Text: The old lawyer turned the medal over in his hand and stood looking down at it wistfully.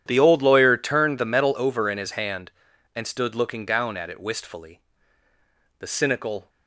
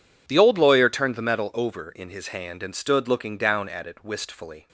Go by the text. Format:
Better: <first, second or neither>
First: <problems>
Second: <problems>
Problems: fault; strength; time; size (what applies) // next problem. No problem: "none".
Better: second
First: goes on to say "The cynical"; noticeable; from 5.7 s on; 0.70 s long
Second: none